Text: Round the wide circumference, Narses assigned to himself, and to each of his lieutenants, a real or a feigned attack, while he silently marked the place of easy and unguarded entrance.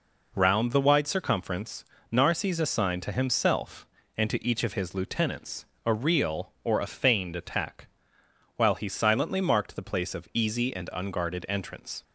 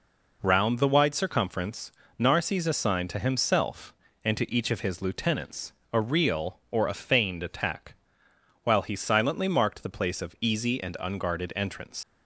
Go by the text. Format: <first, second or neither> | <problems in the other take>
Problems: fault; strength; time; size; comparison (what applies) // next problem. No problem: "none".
first | leaves "entrance" unfinished; at 12.0 s; 75 ms